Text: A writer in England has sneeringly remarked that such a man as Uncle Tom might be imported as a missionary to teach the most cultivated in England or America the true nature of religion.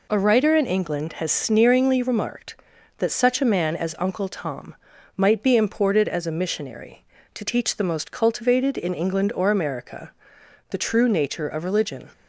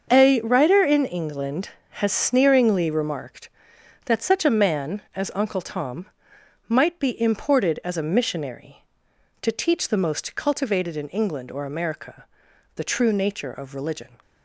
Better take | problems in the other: first | gets quieter; strong; throughout; 10.5 dB // pauses between "Tom" and "might"; noticeable; at 6.0 s; 0.60 s long; also in the first // pauses between "America" and "the"; noticeable; at 12.2 s; 0.52 s long; noticeable in the first

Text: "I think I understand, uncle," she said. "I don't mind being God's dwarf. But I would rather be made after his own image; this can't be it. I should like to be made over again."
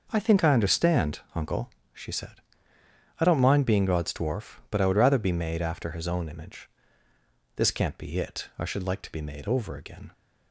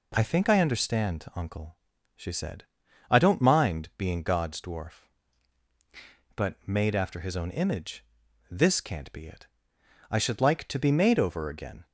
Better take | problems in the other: first | skips "I would rather be"; at 6.6 s

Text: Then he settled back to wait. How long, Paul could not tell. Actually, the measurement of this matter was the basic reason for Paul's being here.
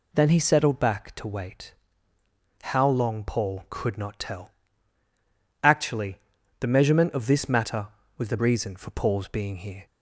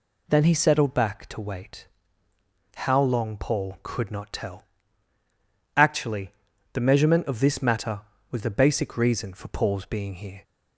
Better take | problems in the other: second | skips "basic"; at 8.3 s

